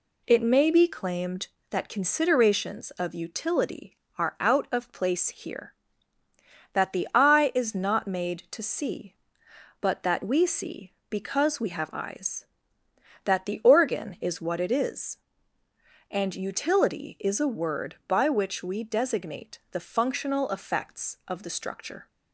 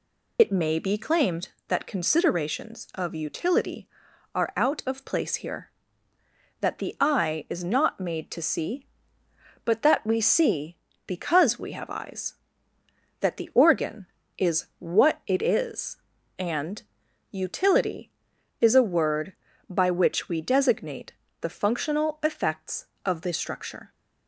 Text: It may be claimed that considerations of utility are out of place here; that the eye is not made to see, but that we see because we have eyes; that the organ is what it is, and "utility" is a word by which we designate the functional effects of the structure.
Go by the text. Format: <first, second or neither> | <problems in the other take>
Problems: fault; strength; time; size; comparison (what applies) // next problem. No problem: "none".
first | loses the start of "It"; at 0.3 s; 70 ms // pauses between "and" and "utility"; noticeable; at 16.8 s; 0.50 s long // pauses between "designate" and "the"; slight; at 21.1 s; 0.30 s long